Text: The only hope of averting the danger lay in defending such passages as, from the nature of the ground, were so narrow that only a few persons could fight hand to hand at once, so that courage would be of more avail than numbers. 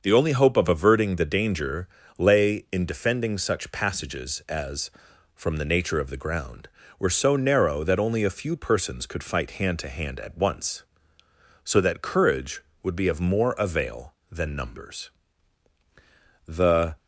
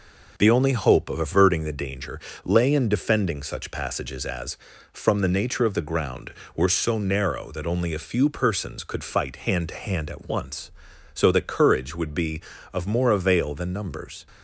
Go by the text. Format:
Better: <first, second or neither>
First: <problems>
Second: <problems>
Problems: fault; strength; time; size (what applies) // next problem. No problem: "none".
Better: second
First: starts louder than the rest; until 1.0 s; 6.5 dB // pauses between "danger" and "lay"; slight; at 1.8 s; 0.30 s long // goes on to say "The"; from 16.4 s on; 0.52 s long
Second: pauses between "danger" and "lay"; slight; at 2.2 s; 0.24 s long